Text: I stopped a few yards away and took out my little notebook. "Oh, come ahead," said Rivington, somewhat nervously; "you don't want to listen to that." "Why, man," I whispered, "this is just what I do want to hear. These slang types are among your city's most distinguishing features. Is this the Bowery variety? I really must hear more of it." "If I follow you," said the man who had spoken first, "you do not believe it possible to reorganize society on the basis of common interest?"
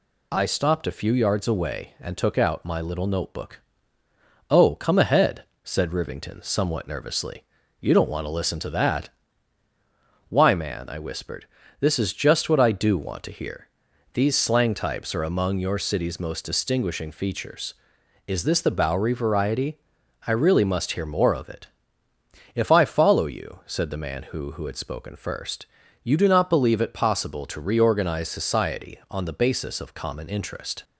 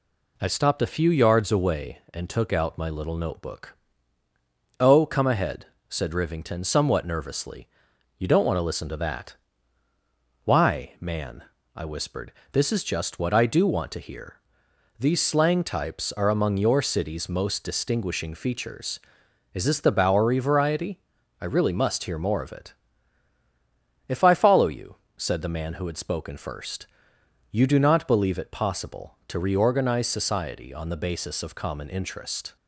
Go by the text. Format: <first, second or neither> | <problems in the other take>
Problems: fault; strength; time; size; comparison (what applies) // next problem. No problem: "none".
second | says "who" twice; at 24.5 s